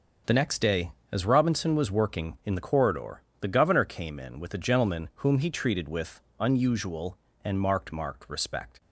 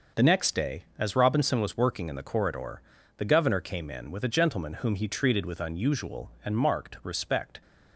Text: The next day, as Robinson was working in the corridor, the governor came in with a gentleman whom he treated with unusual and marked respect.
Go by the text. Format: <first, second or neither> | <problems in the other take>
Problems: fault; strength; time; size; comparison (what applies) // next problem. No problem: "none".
second | starts louder than the rest; noticeable; until 1.4 s; 6 dB; noticeable in the second // pauses between "with" and "unusual"; slight; at 6.2 s; 0.20 s long // says "marked" twice; at 7.9 s